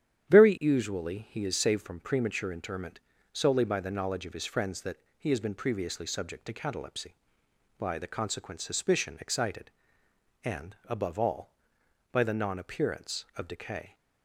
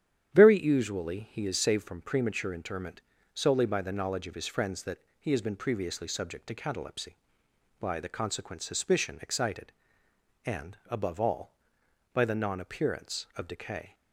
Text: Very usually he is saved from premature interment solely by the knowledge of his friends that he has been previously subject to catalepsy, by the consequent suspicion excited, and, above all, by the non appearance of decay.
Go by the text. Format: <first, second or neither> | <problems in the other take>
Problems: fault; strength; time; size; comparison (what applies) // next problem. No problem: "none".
neither | starts louder than the rest; strong; the same in both // pauses between "interment" and "solely"; slight; the same in both // pauses between "that" and "he"; slight; the same in both